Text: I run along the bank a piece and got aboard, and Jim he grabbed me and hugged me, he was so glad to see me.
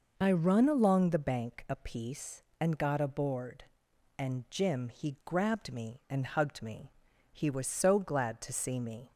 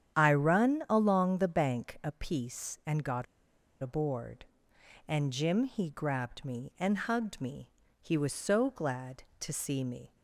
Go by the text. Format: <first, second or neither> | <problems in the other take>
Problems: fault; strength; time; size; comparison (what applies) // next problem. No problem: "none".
first | starts louder than the rest; strong; until 1.2 s; 9.5 dB // pauses between "got" and "aboard"; noticeable; at 3.2 s; 0.58 s long